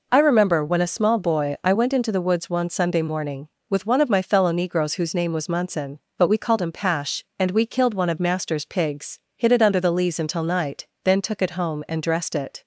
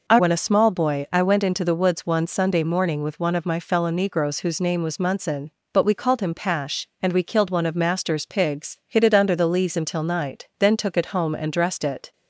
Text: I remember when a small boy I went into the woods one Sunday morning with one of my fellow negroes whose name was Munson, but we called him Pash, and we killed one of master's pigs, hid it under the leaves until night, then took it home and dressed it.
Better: first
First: none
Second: skips "remember"; at 0.1 s

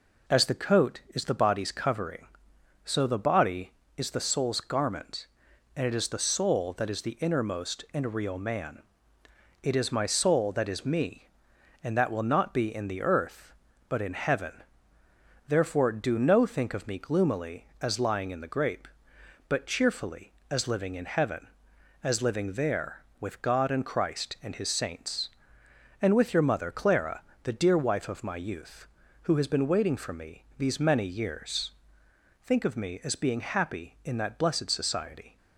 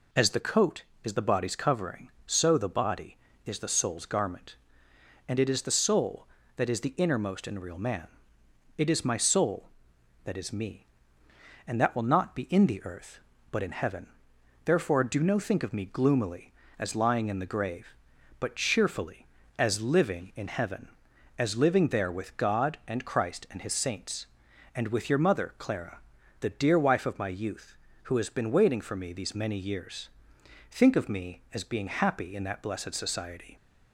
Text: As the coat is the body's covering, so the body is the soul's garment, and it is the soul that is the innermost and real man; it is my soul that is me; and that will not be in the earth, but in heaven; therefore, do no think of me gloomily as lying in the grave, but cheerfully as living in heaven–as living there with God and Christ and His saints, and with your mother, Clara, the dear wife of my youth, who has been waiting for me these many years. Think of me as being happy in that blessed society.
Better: second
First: says "grape" for "grave"; at 18.5 s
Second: none

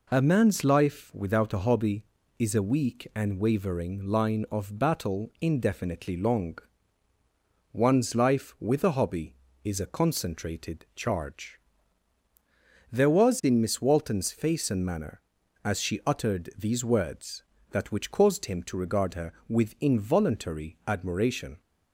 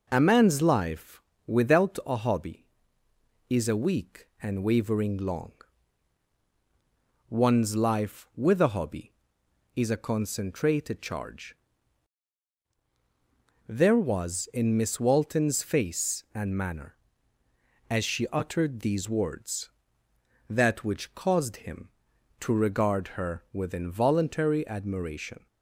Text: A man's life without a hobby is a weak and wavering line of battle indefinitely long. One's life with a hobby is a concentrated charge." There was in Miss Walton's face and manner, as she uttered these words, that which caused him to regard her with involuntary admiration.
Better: first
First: none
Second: pauses between "life" and "without"; slight; at 1.1 s; 0.26 s long // skips "line of battle indefinitely"; at 5.1 s

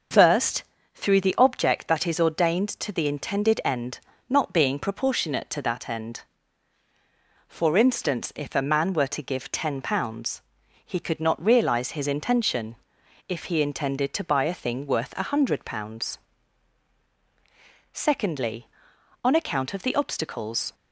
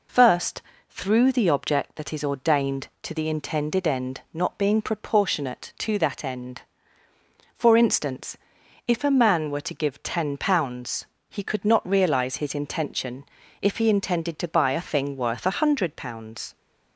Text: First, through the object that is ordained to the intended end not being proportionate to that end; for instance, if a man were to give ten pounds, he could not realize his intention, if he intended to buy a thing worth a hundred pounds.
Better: second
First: starts louder than the rest; until 1.5 s; 6.5 dB // pauses between "end" and "not"; slight; at 3.9 s; 0.28 s long // goes on to say "Secondly on account of the obstacles"; strong; from 17.9 s on; 2.8 s long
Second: none

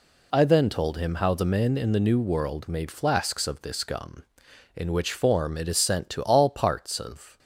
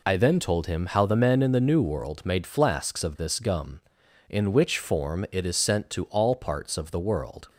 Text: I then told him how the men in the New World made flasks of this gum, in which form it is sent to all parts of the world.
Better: second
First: stops before "the world"; at 7.3 s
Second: none

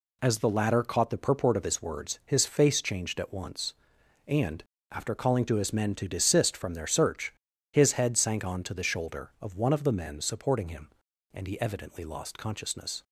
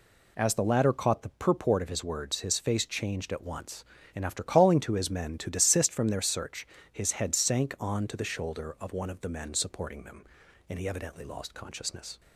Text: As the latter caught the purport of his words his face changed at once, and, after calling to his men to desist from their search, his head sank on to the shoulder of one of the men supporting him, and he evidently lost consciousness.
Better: first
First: none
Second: says "them" for "him"; at 10.0 s

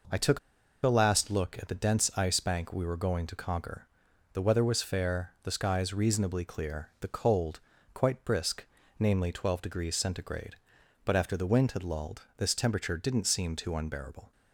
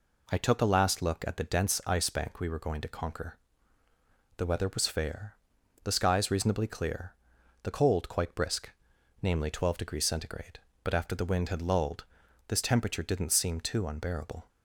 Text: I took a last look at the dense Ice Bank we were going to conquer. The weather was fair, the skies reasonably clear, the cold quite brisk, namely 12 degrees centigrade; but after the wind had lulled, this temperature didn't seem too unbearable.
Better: second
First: pauses between "took" and "a"; at 0.3 s; 0.45 s long // pauses between "cold" and "quite"; slight; at 7.5 s; 0.34 s long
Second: none

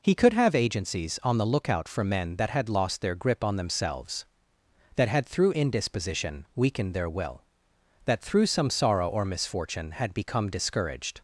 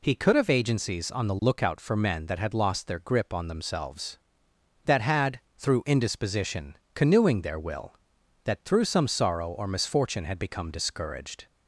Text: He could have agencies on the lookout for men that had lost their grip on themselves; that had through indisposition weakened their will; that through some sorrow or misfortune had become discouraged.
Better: first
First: none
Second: pauses between "had" and "through"; slight; at 5.3 s; 0.18 s long // says "canoeing" for "weakened"; at 6.9 s

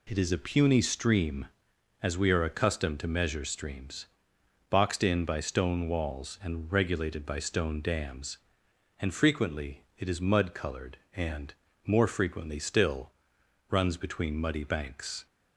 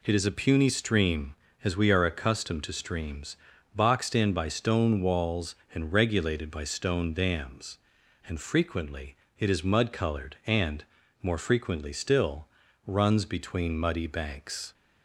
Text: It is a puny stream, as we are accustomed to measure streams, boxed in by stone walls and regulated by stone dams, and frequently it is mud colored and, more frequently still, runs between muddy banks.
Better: first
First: none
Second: skips "measure"; at 2.7 s // pauses between "frequently" and "it"; slight; at 9.1 s; 0.22 s long

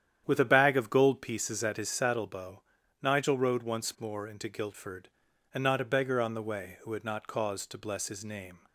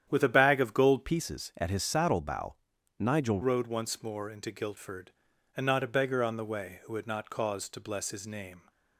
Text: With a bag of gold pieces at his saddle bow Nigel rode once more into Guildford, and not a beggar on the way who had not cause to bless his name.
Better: first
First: starts louder than the rest; strong; until 1.2 s; 9.5 dB // pauses between "bow" and "Nigel"; at 2.6 s; 0.40 s long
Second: starts louder than the rest; strong; until 1.1 s; 9.5 dB // changes voice from "pieces" to "Nigel"; from 1.0 to 3.4 s; 2.4 s long // pauses between "bow" and "Nigel"; at 2.5 s; 0.44 s long

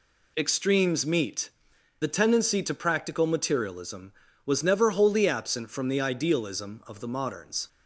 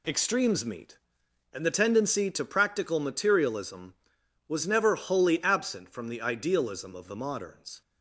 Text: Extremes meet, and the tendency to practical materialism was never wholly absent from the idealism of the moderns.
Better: second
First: skips "and"; at 1.7 s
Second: none

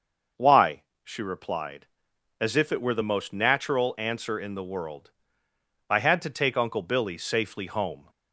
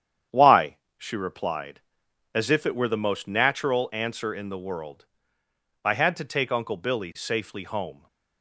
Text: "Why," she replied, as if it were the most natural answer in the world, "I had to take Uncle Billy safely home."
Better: first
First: starts louder than the rest; until 1.5 s; 6.5 dB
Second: gets quieter; noticeable; throughout; 6 dB // starts louder than the rest; strong; until 1.5 s; 9 dB

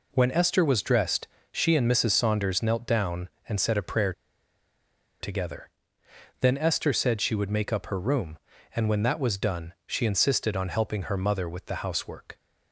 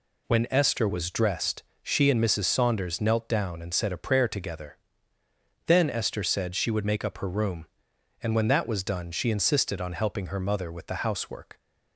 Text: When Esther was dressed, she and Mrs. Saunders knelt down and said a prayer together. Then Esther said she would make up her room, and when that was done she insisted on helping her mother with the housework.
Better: second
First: pauses between "prayer" and "together"; at 4.1 s; 1.0 s long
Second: none

